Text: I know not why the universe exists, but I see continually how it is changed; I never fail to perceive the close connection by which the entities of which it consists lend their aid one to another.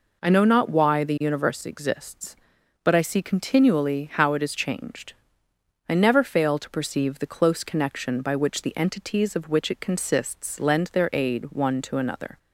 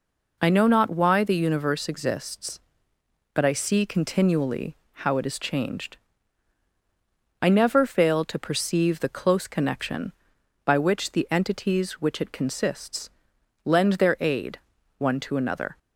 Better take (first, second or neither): first